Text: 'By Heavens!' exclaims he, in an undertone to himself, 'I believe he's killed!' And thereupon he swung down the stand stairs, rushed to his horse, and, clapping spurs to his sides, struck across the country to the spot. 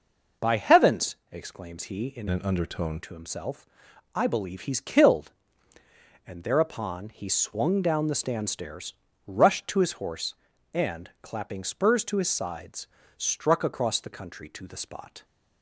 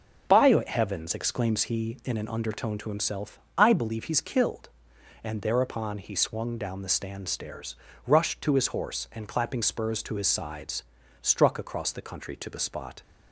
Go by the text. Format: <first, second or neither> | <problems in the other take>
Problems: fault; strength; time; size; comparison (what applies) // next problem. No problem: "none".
second | changes voice from "an" to "undertone"; from 2.2 to 2.9 s; 0.7 s long